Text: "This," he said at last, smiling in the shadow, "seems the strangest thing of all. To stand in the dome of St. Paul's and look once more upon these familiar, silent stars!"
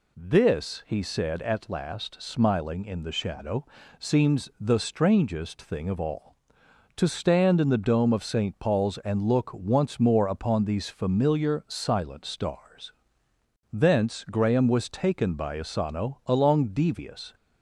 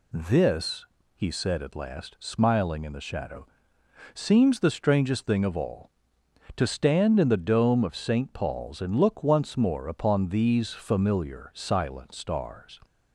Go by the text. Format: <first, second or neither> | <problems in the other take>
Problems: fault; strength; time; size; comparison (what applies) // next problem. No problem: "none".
second | goes on to say "Thence Graham was taken by Asano along devious"; strong; from 13.7 s on; 3.6 s long